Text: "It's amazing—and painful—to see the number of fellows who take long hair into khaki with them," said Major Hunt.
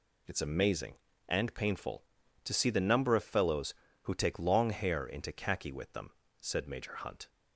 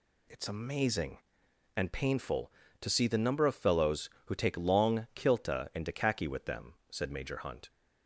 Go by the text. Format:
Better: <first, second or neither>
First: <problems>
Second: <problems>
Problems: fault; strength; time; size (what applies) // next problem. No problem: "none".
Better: first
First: none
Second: says "kilta" for "hair"; at 5.1 s